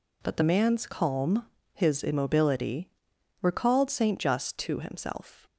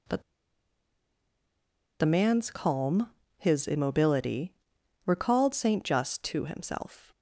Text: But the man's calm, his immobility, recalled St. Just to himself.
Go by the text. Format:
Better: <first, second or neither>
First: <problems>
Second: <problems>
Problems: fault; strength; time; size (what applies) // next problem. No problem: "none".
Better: first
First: none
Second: pauses between "But" and "the"; strong; at 0.2 s; 1.7 s long